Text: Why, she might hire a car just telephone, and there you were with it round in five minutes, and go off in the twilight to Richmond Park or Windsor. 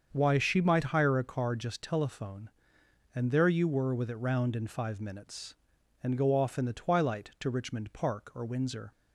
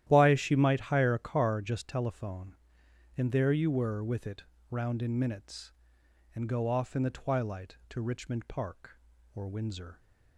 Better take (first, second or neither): first